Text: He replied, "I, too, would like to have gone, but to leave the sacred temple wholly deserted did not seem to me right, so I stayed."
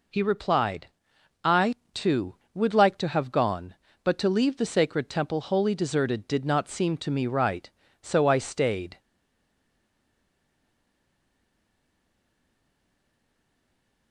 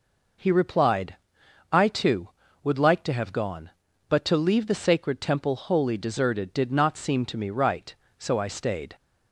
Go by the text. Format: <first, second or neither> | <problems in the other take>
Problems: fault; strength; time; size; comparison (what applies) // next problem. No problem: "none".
second | stays silent after the last word; strong; from 8.9 s on; 5.2 s long